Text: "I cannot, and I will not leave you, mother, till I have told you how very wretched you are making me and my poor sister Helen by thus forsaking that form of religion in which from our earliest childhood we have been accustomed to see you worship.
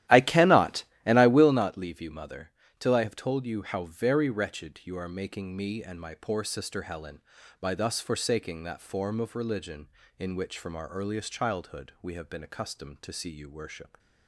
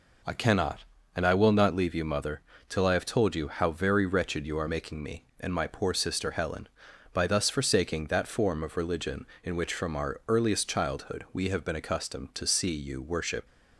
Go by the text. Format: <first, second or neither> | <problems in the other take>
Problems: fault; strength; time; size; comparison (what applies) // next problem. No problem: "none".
second | starts louder than the rest; strong; until 1.6 s; 13.5 dB